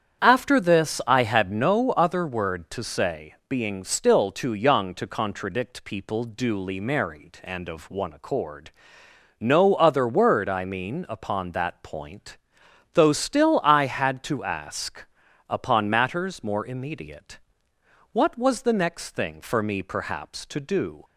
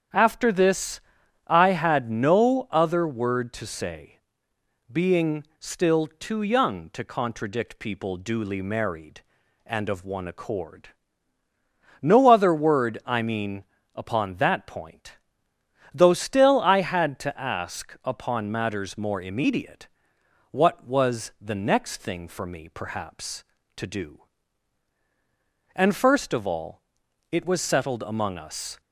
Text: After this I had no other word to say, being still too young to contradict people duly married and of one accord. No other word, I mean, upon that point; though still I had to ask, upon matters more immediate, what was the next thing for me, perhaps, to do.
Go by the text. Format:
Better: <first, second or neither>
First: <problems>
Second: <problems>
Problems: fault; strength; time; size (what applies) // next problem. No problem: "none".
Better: first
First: starts louder than the rest; strong; until 1.2 s; 8.5 dB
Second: starts louder than the rest; strong; until 1.6 s; 8.5 dB // pauses between "this" and "I"; noticeable; at 0.9 s; 0.48 s long // goes on to say "And first of all it was settled among us"; strong; from 25.7 s on; 3.0 s long